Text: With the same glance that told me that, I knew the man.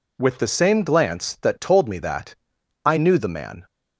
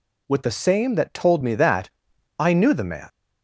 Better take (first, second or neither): first